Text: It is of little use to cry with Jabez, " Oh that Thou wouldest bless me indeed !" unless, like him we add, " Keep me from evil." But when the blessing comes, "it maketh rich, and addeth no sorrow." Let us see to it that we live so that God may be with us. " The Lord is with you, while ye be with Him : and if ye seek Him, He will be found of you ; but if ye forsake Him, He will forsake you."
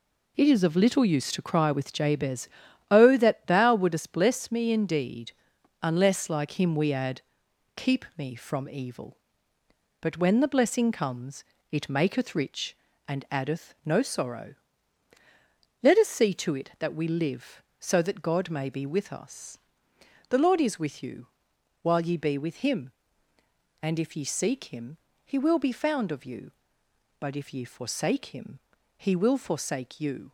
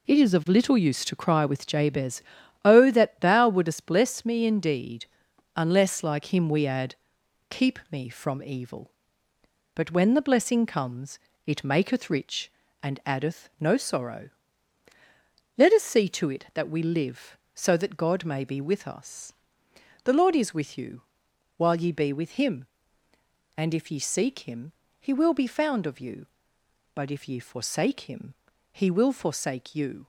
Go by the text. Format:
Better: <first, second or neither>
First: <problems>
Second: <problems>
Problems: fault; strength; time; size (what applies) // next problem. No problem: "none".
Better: neither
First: none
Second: none